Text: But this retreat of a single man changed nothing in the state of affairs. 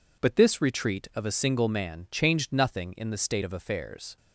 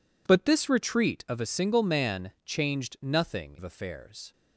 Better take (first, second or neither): first